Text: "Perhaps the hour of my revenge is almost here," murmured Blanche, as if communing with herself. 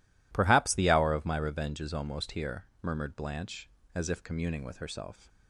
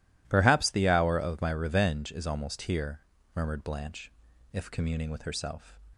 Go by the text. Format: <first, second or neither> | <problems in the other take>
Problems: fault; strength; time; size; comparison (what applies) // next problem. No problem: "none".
first | skips "as"; at 4.3 s